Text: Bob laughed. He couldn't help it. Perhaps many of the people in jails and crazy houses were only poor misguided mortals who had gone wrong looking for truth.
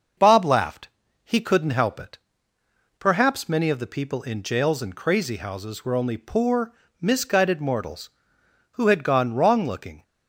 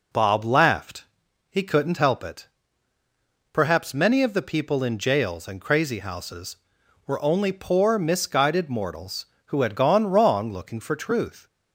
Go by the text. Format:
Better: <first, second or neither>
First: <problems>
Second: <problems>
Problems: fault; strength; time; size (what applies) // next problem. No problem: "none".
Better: second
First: starts louder than the rest; until 1.5 s; 6 dB // pauses between "poor" and "misguided"; slight; at 6.7 s; 0.26 s long // stops before "for truth"; at 10.0 s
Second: none